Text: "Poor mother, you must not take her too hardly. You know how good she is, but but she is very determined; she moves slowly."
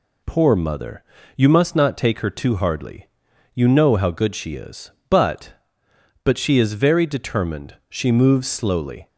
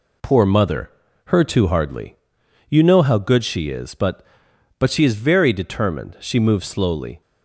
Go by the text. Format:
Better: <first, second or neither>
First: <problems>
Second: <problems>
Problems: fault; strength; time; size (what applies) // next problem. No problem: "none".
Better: first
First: none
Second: skips "you must not take"; at 1.0 s